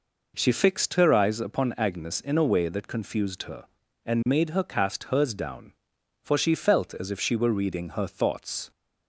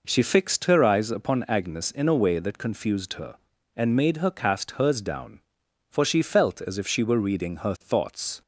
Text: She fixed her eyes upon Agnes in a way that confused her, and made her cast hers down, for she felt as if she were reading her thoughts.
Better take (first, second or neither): neither